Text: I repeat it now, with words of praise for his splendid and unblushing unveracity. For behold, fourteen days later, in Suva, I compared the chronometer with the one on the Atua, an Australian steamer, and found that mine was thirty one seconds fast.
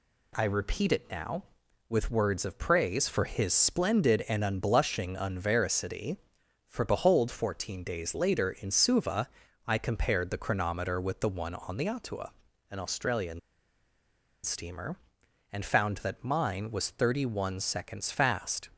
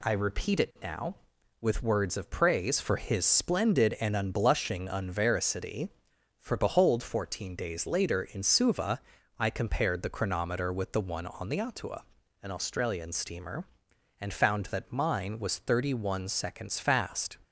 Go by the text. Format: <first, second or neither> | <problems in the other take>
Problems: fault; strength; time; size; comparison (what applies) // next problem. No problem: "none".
second | pauses between "Australian" and "steamer"; at 13.3 s; 1.0 s long